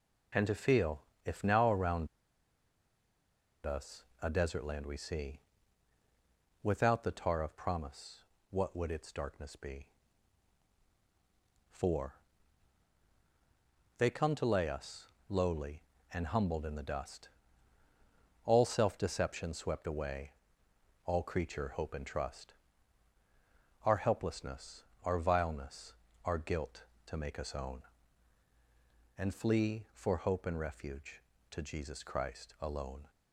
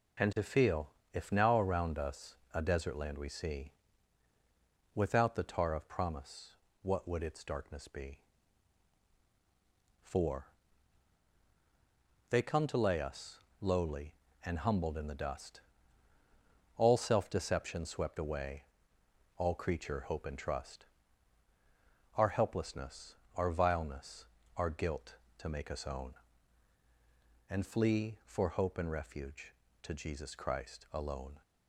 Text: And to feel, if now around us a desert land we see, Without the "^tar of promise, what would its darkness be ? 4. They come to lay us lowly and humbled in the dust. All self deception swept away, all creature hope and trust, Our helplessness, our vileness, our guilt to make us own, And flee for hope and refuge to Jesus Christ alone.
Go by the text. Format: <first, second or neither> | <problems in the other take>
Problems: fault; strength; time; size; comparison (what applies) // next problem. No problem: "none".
second | pauses between "around" and "us"; strong; at 2.0 s; 1.5 s long // pauses between "us" and "a"; slight; at 4.0 s; 0.18 s long; slight in the second // pauses between "us" and "lowly"; slight; at 15.0 s; 0.22 s long; slight in the second